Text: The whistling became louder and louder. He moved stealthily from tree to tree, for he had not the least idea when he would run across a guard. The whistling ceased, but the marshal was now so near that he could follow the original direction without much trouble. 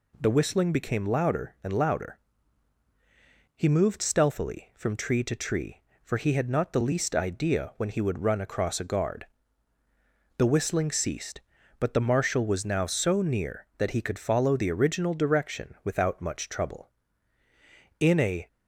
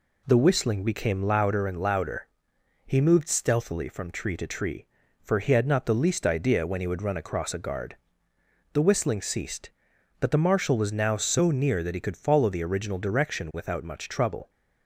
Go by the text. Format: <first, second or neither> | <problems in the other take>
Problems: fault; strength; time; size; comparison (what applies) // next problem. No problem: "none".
second | goes on to say "In a"; slight; from 17.9 s on; 0.48 s long